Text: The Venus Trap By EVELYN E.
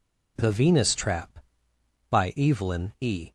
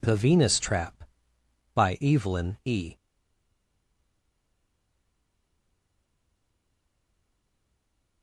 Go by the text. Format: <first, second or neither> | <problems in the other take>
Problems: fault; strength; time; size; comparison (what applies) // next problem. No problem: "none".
first | stays silent after the last word; strong; from 2.9 s on; 5.3 s long